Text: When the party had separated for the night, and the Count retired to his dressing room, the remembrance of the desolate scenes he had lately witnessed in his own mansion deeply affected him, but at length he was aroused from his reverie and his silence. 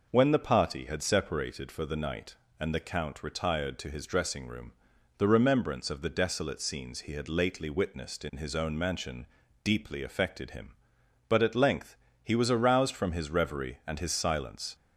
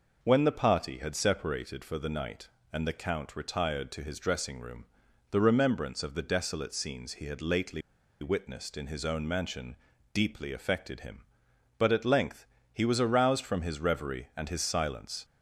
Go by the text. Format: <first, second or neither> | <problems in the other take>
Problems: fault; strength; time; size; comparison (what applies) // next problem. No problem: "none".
first | pauses between "lately" and "witnessed"; at 7.8 s; 0.40 s long // pauses between "mansion" and "deeply"; at 9.7 s; 0.38 s long; also in the first // pauses between "length" and "he"; slight; at 12.4 s; 0.30 s long; slight in the first